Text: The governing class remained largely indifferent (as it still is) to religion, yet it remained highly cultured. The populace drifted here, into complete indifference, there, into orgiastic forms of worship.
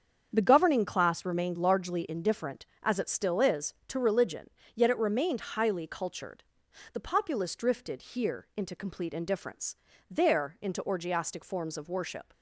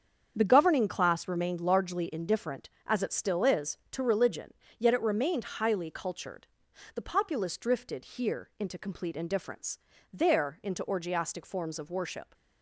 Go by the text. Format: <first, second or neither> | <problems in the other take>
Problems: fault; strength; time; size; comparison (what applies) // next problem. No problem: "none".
neither | starts louder than the rest; strong; the same in both